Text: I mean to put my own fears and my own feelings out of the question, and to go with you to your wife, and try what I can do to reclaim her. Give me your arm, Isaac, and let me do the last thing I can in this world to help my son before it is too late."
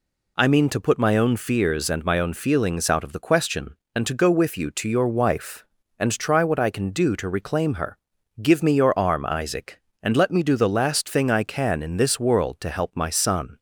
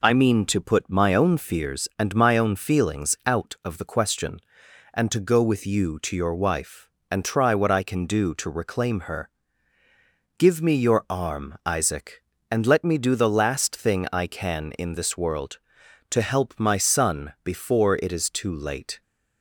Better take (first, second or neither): second